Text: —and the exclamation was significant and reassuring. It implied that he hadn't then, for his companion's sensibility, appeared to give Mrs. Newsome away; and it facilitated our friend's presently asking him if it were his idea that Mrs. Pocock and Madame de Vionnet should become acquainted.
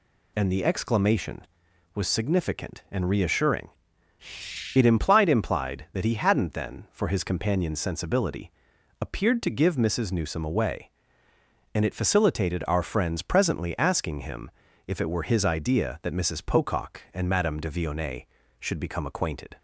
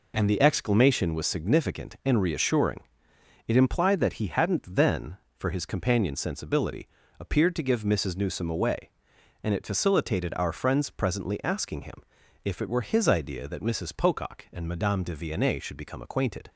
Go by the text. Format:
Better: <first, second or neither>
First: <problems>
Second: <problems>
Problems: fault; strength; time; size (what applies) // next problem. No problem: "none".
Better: second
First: says "implied" twice; at 5.2 s // pauses between "him" and "if"; at 14.4 s; 0.38 s long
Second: pauses between "him" and "if"; at 12.0 s; 0.44 s long